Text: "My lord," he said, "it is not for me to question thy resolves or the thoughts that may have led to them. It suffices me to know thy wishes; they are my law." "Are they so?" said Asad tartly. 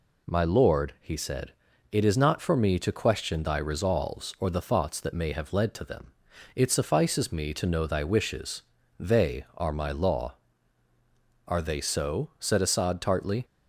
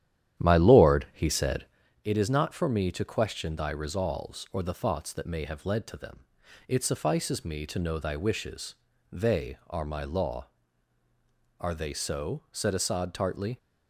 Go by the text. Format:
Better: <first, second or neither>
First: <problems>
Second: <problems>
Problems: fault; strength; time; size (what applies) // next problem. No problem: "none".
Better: first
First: none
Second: starts louder than the rest; strong; until 1.9 s; 11 dB